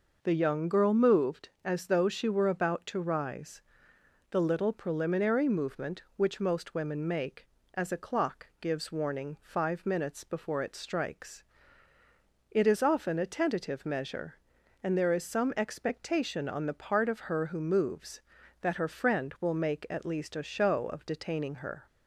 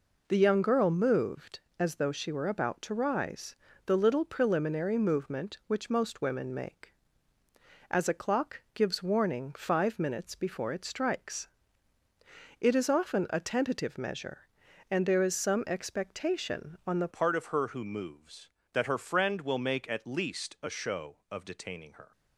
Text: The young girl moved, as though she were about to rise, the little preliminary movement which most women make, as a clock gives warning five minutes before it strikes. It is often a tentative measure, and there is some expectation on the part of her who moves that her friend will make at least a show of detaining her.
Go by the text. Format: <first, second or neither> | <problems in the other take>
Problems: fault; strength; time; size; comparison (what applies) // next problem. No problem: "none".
first | changes voice at "part"; from 17.1 s on; 5.0 s long